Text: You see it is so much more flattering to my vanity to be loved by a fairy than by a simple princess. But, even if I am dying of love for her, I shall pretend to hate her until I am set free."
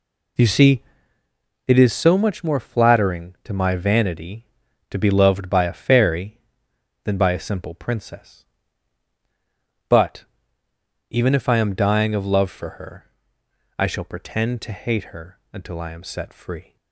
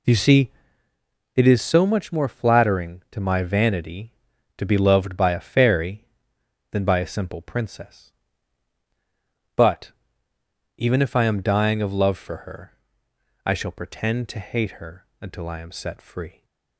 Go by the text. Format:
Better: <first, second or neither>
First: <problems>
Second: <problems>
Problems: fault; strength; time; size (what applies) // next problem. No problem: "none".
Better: neither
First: pauses between "see" and "it"; noticeable; at 0.8 s; 0.84 s long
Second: pauses between "see" and "it"; noticeable; at 0.5 s; 0.84 s long